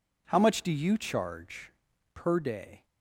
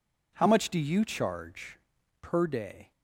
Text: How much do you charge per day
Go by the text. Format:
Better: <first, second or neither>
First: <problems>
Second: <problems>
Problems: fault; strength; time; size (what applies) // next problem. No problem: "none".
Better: neither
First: pauses between "charge" and "per"; at 1.7 s; 0.43 s long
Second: pauses between "charge" and "per"; at 1.7 s; 0.44 s long